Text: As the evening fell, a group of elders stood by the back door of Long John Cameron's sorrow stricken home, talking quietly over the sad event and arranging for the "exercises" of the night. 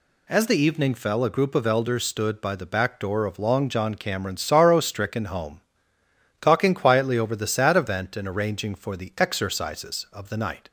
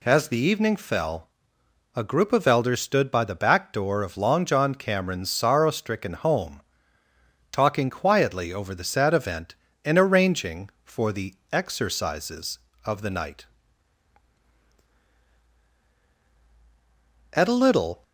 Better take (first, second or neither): first